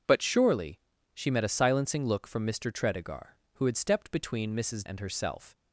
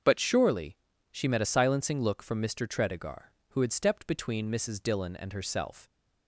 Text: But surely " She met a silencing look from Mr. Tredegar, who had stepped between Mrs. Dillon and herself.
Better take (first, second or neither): second